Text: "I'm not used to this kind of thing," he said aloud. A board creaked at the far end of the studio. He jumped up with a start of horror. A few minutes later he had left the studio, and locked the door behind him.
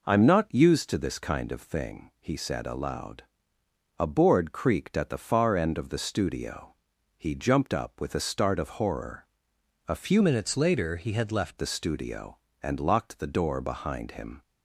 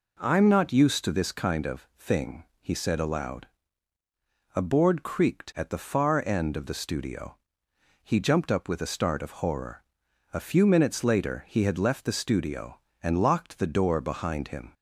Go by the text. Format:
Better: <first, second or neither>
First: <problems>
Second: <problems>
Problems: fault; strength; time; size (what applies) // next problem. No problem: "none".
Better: second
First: changes voice from "minutes" to "left"; from 10.2 to 11.5 s; 1.3 s long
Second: none